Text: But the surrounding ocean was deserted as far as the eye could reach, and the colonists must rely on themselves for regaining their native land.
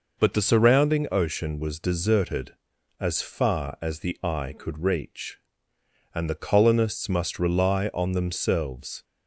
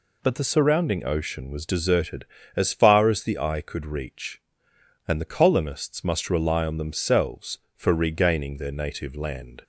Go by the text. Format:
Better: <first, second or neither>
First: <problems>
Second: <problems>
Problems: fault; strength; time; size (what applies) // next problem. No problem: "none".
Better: second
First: stops before "for regaining their native land"; at 9.0 s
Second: none